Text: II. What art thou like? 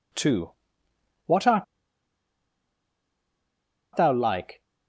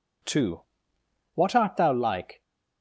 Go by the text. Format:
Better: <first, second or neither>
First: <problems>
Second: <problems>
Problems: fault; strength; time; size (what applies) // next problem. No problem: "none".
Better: second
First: pauses between "art" and "thou"; strong; at 1.6 s; 2.3 s long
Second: none